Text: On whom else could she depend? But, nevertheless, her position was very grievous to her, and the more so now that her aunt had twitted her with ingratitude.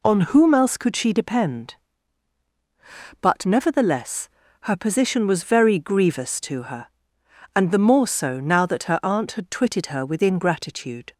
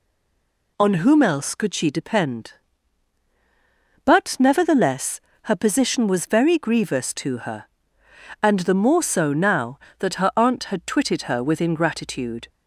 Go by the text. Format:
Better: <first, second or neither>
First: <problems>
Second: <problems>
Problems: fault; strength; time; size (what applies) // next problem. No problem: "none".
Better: first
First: none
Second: stays silent before the first word; slight; until 0.7 s; 0.7 s long